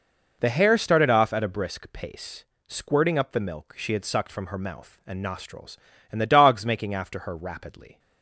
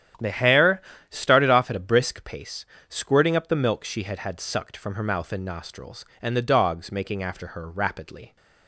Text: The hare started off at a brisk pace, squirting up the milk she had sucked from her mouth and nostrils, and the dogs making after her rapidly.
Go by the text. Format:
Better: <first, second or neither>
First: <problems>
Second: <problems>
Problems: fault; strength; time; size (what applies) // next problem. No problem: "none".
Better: first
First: none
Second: starts louder than the rest; strong; until 1.4 s; 10 dB // pauses between "hare" and "started"; slight; at 0.8 s; 0.28 s long // says "had" twice; at 4.1 s